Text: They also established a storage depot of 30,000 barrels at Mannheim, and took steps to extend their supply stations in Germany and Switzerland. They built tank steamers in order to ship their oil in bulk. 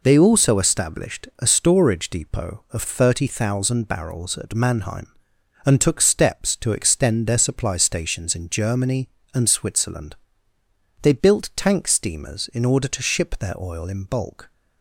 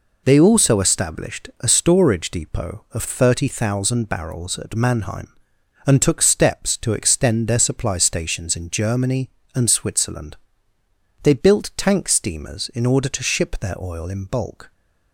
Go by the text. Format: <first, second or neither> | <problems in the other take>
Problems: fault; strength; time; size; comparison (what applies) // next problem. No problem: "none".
neither | none